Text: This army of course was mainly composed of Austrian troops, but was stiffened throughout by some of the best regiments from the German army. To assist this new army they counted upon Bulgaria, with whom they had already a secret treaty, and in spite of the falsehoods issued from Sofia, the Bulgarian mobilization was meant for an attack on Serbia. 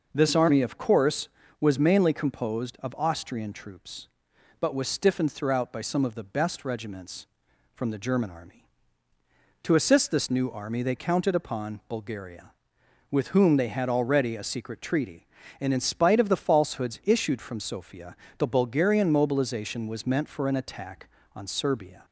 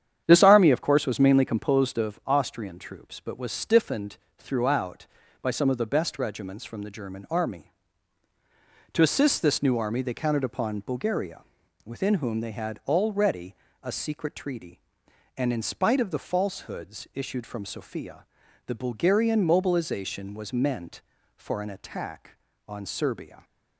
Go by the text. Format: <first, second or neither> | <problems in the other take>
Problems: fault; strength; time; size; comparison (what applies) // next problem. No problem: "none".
first | starts louder than the rest; strong; until 1.2 s; 9 dB // pauses between "stiffened" and "throughout"; slight; at 4.1 s; 0.22 s long // says "within" for "with"; at 11.8 s // pauses between "already" and "a"; slight; at 13.5 s; 0.28 s long